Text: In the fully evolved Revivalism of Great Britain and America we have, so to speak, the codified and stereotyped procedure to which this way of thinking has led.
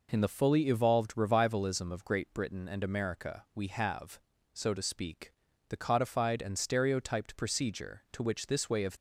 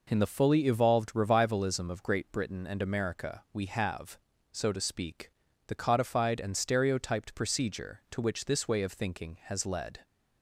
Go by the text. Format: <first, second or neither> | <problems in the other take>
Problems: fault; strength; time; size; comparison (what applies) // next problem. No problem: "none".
second | stops before "thinking has led"; at 8.9 s